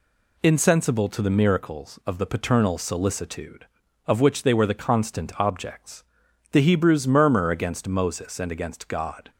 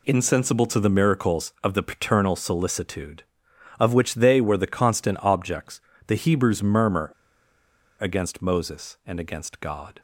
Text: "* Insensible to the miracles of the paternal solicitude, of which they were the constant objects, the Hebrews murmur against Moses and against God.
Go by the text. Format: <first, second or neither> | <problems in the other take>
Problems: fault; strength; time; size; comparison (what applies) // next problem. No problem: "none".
first | pauses between "murmur" and "against"; noticeable; at 7.1 s; 0.89 s long